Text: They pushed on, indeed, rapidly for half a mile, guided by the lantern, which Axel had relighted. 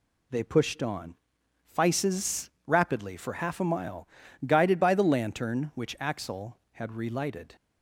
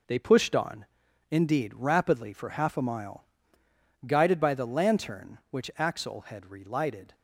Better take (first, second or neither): second